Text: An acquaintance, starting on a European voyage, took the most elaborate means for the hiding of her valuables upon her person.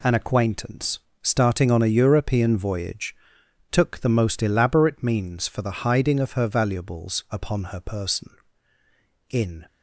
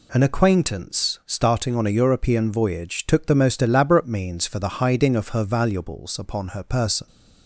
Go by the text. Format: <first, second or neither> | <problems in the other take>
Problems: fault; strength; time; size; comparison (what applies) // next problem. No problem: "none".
second | goes on to say "In"; slight; from 9.2 s on; 0.36 s long